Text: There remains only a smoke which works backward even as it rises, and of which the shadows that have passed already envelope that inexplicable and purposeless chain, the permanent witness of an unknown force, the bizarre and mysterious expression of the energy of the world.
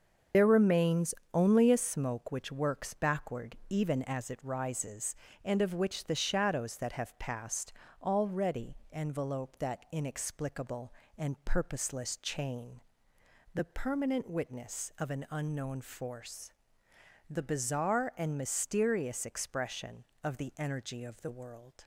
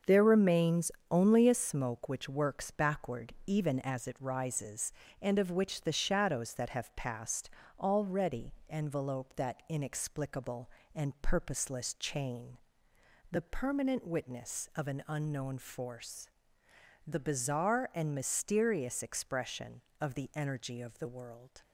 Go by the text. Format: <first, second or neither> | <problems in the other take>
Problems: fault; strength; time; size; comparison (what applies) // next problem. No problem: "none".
second | loses the start of "There"; at 0.3 s; 80 ms // starts louder than the rest; until 1.5 s; 6.5 dB; also in the second // pauses between "remains" and "only"; slight; at 1.1 s; 0.20 s long; slight in the second // pauses between "passed" and "already"; slight; at 7.7 s; 0.28 s long; slight in the second